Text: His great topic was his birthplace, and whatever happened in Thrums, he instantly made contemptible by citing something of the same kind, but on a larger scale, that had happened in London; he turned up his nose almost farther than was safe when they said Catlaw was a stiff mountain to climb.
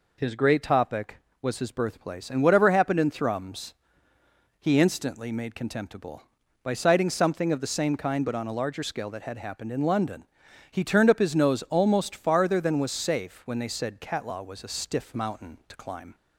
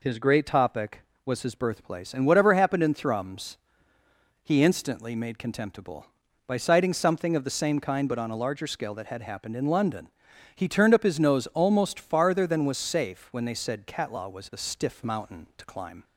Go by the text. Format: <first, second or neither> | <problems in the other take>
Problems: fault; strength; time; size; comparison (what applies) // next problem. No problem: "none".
neither | none